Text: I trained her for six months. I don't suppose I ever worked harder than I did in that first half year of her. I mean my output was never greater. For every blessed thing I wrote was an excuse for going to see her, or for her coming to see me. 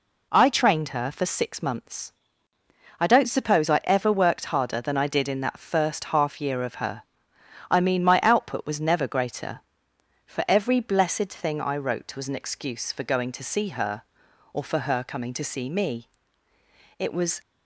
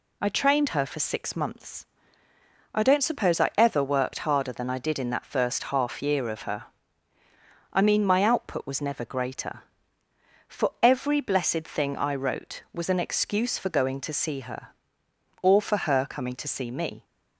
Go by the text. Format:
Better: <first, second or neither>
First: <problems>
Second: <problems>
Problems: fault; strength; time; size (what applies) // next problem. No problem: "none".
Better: second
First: goes on to say "It was"; slight; from 16.9 s on; 0.42 s long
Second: none